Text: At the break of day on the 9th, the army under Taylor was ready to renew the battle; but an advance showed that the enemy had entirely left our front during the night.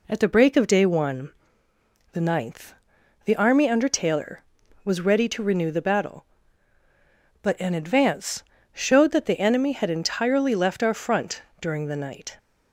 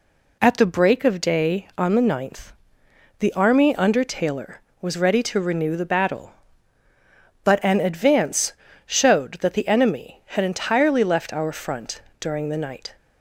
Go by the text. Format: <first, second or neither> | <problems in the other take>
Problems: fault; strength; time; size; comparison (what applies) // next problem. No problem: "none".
second | says "one" for "on"; at 0.8 s // pauses between "advance" and "showed"; slight; at 8.4 s; 0.28 s long; slight in the second // pauses between "front" and "during"; slight; at 11.4 s; 0.18 s long; slight in the second